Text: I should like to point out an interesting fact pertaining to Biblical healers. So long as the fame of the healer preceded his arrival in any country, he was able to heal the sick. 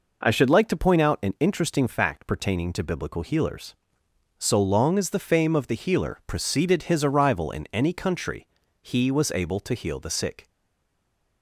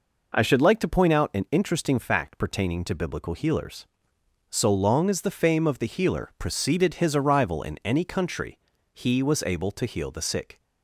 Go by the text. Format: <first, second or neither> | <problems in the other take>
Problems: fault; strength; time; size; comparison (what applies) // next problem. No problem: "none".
second | stays silent after the last word; from 10.4 s on; 1.0 s long